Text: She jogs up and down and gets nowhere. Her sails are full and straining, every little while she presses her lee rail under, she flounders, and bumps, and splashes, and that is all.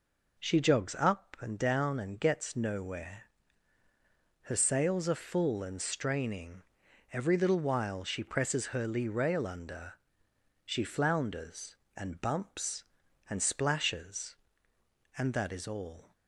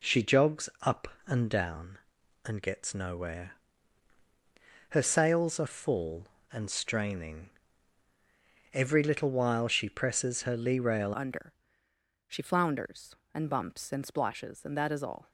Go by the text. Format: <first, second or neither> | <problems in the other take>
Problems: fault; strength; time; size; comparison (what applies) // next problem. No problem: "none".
first | changes voice at "under"; from 11.1 s on; 4.2 s long